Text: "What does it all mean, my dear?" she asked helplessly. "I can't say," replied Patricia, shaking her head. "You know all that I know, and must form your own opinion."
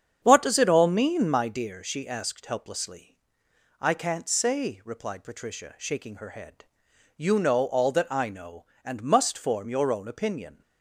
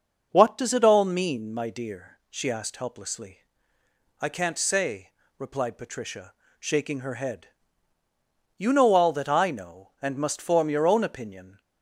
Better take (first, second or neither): second